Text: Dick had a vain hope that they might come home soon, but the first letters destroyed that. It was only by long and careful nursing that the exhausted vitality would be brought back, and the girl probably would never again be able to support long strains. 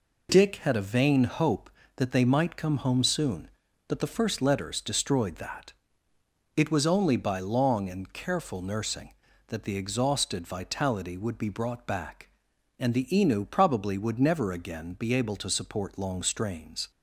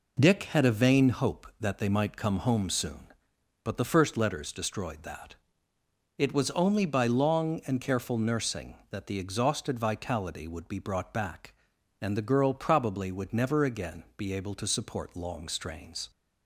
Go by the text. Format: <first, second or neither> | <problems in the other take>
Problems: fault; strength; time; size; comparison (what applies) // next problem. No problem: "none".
second | says "inu" for "girl"; at 13.1 s